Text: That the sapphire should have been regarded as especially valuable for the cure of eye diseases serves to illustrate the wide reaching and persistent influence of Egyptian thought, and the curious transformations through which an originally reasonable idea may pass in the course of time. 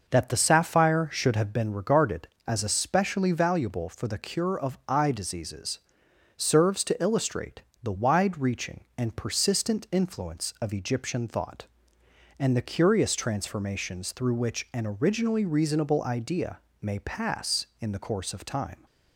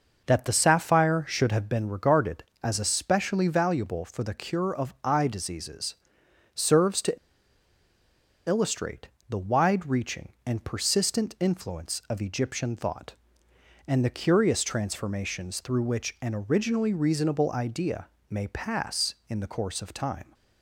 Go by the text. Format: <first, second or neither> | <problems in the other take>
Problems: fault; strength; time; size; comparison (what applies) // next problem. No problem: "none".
first | starts louder than the rest; noticeable; until 1.2 s; 6 dB; noticeable in the first // pauses between "diseases" and "serves"; noticeable; at 5.9 s; 0.60 s long; noticeable in the first // pauses between "to" and "illustrate"; strong; at 7.1 s; 1.3 s long // pauses between "illustrate" and "the"; slight; at 9.0 s; 0.20 s long; slight in the first // pauses between "idea" and "may"; slight; at 18.0 s; 0.22 s long; slight in the first